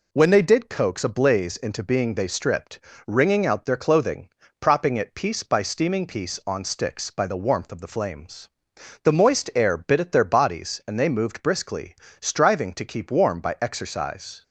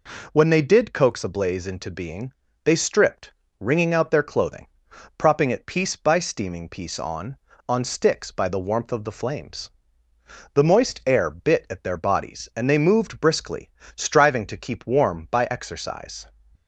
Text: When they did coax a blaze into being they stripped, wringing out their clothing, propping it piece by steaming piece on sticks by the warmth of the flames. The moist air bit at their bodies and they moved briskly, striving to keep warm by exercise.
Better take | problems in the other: first | pauses between "being" and "they"; slight; at 2.3 s; 0.30 s long // says "on" twice; at 7.6 s

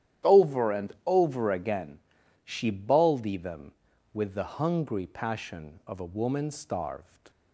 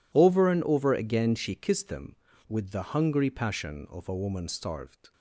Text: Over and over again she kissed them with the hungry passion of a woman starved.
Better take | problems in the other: second | starts louder than the rest; strong; until 1.4 s; 11 dB // pauses between "and" and "over"; slight; at 0.8 s; 0.16 s long // pauses between "again" and "she"; noticeable; at 1.9 s; 0.48 s long // says "baldy" for "kissed"; at 2.6 s

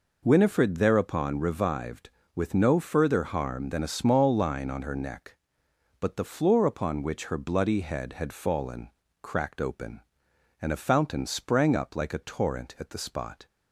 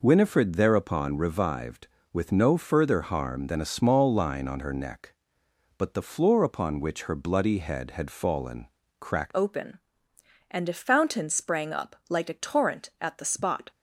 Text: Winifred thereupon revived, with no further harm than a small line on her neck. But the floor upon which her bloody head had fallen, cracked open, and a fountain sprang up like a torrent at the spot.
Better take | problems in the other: first | changes voice at "open"; from 9.3 s on; 4.4 s long

